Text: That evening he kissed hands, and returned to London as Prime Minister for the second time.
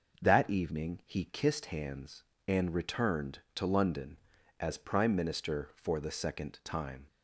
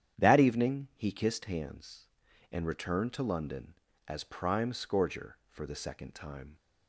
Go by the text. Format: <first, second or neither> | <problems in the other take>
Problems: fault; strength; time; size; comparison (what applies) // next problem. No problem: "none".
first | starts louder than the rest; strong; until 1.2 s; 9.5 dB // says "Scourger" for "Minister"; at 4.7 s